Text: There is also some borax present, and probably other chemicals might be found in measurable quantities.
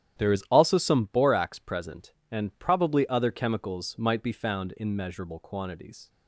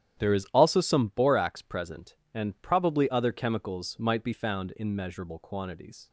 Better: neither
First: starts louder than the rest; strong; until 1.2 s; 11 dB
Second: starts louder than the rest; strong; until 1.2 s; 10.5 dB

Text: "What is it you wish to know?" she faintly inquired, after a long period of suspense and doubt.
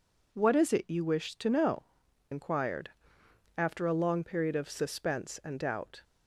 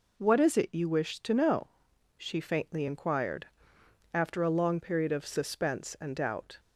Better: second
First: skips "she faintly"; at 2.0 s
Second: none

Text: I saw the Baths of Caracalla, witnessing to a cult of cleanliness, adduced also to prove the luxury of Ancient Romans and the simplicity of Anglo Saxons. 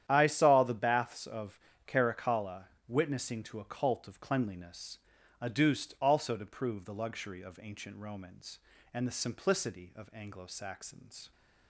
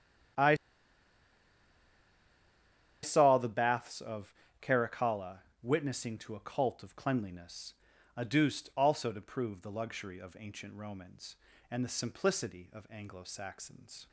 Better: first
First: starts louder than the rest; strong; until 1.1 s; 10 dB // pauses between "of" and "Caracalla"; slight; at 1.5 s; 0.30 s long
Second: starts louder than the rest; strong; until 3.8 s; 10 dB // pauses between "I" and "saw"; strong; at 0.5 s; 2.4 s long // pauses between "of" and "Caracalla"; slight; at 4.3 s; 0.30 s long

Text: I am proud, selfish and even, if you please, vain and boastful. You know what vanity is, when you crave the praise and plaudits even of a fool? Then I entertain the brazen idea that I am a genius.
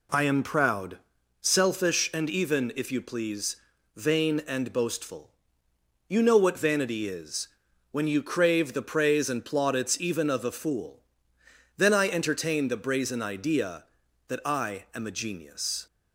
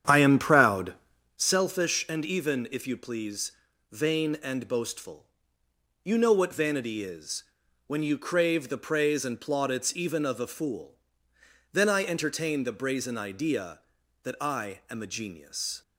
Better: first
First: none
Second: starts louder than the rest; strong; until 1.5 s; 9 dB

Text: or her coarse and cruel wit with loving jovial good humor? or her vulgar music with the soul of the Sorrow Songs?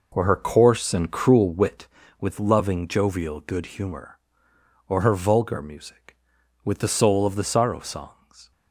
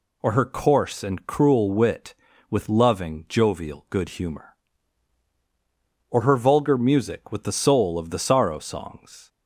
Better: second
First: starts louder than the rest; noticeable; until 2.0 s; 5 dB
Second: none

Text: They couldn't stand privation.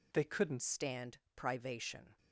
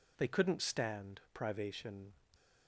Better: second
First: changes voice at "stand"; from 0.6 s on; 1.5 s long // pauses between "stand" and "privation"; slight; at 1.1 s; 0.16 s long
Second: none

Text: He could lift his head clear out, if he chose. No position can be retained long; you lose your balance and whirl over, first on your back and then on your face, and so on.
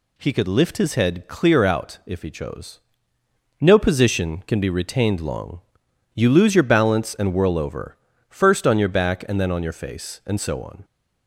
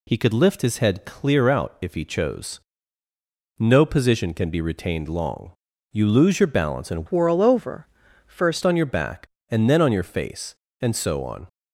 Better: first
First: none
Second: changes voice from "whirl" to "first"; from 7.0 to 8.6 s; 1.6 s long

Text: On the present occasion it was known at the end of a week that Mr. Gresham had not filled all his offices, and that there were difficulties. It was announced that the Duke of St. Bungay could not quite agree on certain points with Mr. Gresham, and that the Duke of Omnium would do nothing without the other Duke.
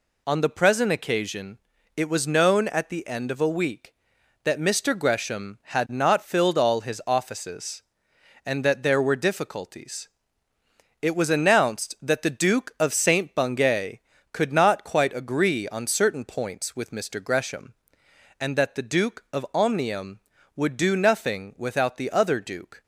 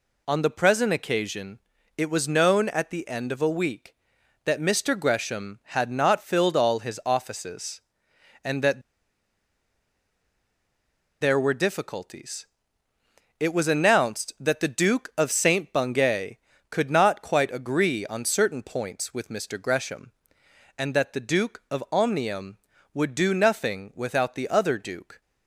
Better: first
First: pauses between "occasion" and "it"; at 1.5 s; 0.40 s long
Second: pauses between "occasion" and "it"; at 1.5 s; 0.40 s long // pauses between "that" and "there"; strong; at 8.8 s; 2.3 s long

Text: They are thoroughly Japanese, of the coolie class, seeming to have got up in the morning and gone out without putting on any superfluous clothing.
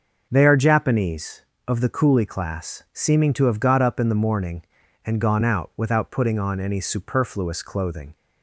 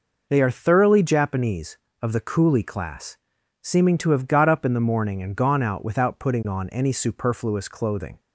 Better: second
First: starts louder than the rest; noticeable; until 1.3 s; 6 dB // skips "thoroughly"; at 0.5 s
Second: none

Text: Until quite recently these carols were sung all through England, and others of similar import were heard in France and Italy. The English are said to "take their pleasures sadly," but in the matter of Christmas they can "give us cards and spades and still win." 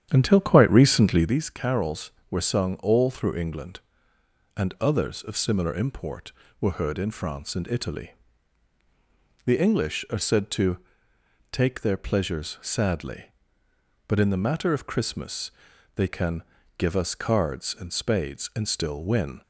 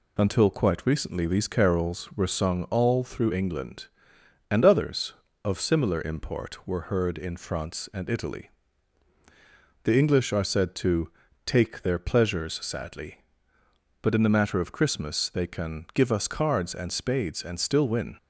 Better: second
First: starts louder than the rest; strong; until 1.4 s; 9.5 dB // pauses between "to" and "take"; noticeable; at 10.7 s; 0.74 s long // pauses between "Christmas" and "they"; noticeable; at 15.5 s; 0.46 s long // pauses between "can" and "give"; slight; at 16.4 s; 0.35 s long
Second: pauses between "to" and "take"; slight; at 11.0 s; 0.34 s long

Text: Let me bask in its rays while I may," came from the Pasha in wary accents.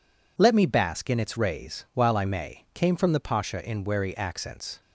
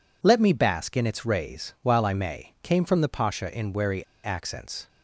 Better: first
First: none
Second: pauses between "wary" and "accents"; slight; at 4.0 s; 0.19 s long

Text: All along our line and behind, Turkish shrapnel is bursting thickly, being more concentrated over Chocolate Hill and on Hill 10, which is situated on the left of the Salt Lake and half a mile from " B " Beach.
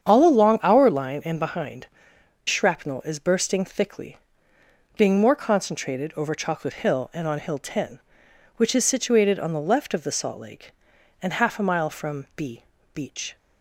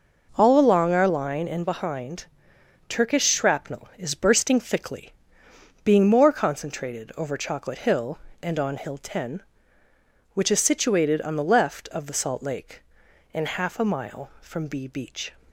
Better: second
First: starts louder than the rest; strong; until 1.1 s; 8 dB // skips "Turkish"; at 2.1 s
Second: none

